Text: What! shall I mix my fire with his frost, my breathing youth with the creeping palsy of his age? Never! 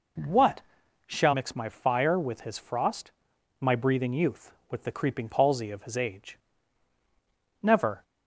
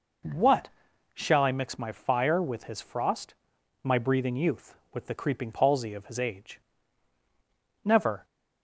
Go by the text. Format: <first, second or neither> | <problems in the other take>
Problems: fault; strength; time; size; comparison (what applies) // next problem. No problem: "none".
second | skips "I"; at 1.3 s